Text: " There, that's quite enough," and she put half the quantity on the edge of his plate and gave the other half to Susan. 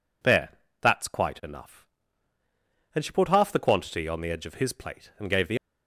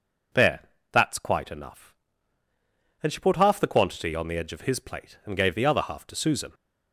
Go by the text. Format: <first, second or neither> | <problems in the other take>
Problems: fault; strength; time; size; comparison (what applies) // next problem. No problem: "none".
second | stops before "other half to Susan"; at 5.5 s